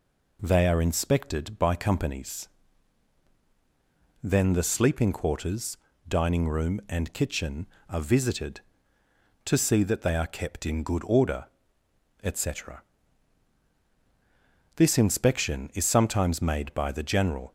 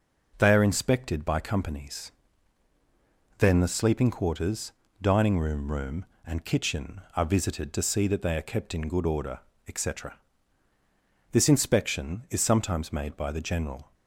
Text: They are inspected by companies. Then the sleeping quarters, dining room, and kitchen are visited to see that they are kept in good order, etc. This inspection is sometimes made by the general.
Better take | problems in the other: first | says "room" twice; at 5.7 s

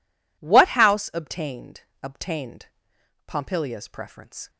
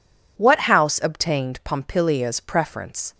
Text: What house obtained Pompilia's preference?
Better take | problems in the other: second | says "obtained" twice; at 2.0 s

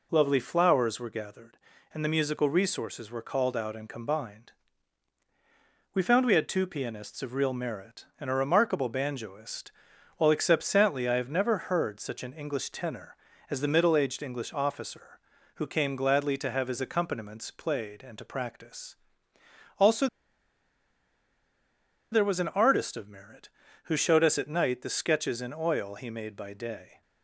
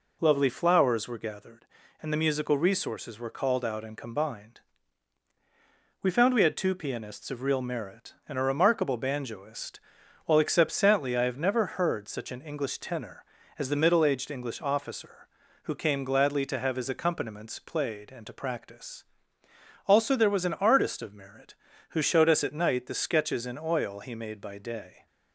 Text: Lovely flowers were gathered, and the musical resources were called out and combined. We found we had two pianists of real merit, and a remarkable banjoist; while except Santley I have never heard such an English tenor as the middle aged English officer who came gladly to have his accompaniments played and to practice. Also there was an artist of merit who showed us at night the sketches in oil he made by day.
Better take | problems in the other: second | pauses between "Also" and "there"; strong; at 20.0 s; 2.0 s long

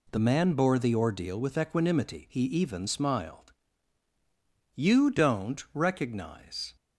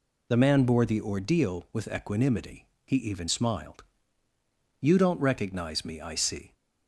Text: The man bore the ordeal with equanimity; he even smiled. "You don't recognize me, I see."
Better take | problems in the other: second | stops before "me I see"; at 6.7 s

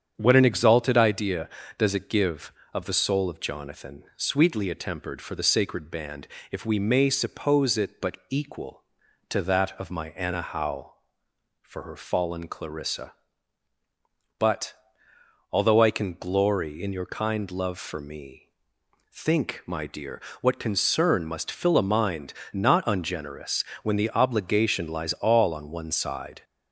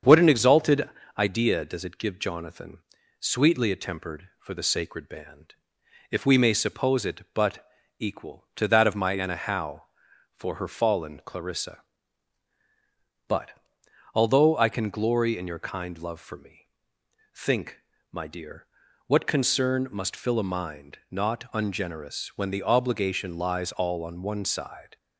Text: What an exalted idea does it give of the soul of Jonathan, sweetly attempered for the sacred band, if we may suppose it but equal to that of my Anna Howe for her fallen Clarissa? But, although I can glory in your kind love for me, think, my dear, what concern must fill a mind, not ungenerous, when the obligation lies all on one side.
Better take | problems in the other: first | starts louder than the rest; strong; until 1.3 s; 7 dB; strong in the first // pauses between "exalted" and "idea"; slight; at 0.8 s; 0.30 s long // skips "of the soul of"; at 2.1 s // pauses between "but" and "equal"; slight; at 7.6 s; 0.34 s long

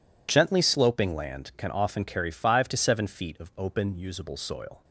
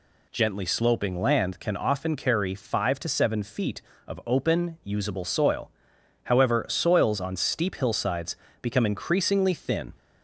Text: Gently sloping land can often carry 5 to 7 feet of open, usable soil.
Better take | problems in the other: first | goes on to say "However soils on steep hillsides become increasingly thin"; strong; from 6.2 s on; 3.7 s long

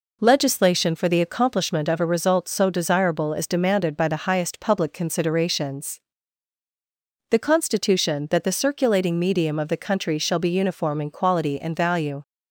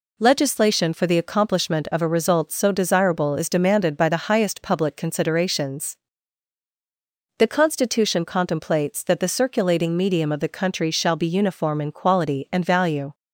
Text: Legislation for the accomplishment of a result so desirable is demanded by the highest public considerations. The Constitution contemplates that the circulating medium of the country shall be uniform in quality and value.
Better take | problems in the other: second | skips "contemplates"; at 8.2 s

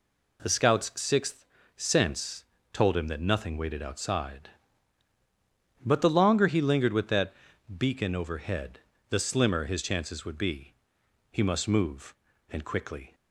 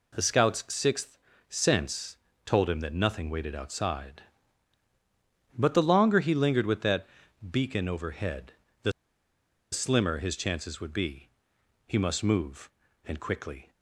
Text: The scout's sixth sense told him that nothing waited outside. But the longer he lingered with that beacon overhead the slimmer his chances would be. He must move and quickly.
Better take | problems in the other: first | pauses between "sixth" and "sense"; slight; at 1.1 s; 0.32 s long; slight in the first // pauses between "sense" and "told"; slight; at 2.1 s; 0.28 s long; slight in the first // pauses between "that" and "beacon"; at 7.0 s; 0.44 s long; also in the first // pauses between "overhead" and "the"; slight; at 8.5 s; 0.30 s long; slight in the first // pauses between "the" and "slimmer"; noticeable; at 8.9 s; 0.80 s long

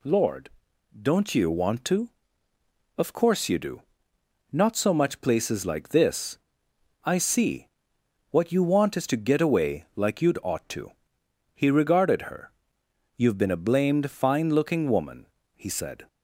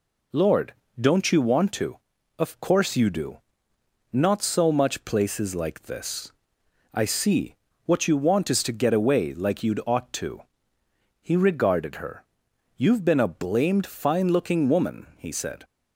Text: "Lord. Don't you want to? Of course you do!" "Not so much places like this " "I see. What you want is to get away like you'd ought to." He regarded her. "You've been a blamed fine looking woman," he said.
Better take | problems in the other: neither | none

